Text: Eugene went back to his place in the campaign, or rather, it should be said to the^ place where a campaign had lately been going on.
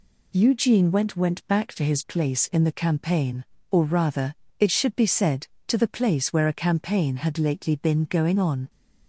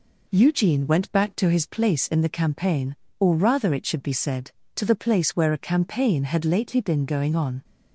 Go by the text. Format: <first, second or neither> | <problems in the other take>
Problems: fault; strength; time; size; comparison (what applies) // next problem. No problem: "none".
second | says "went" twice; at 1.1 s